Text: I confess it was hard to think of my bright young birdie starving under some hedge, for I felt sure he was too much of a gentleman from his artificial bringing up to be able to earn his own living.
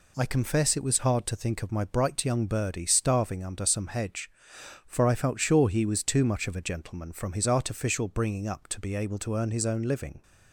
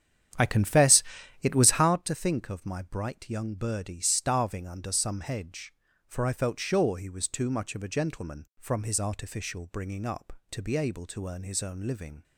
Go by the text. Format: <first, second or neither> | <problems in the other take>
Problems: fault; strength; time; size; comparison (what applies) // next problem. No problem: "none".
first | starts louder than the rest; strong; until 1.9 s; 9.5 dB // pauses between "confess" and "it"; at 1.0 s; 0.40 s long